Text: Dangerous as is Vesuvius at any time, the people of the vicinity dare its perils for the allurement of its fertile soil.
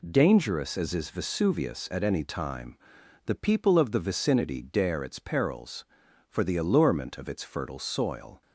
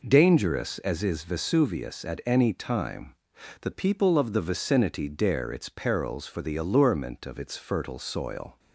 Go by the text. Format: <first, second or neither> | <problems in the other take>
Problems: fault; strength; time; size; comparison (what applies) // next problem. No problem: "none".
neither | none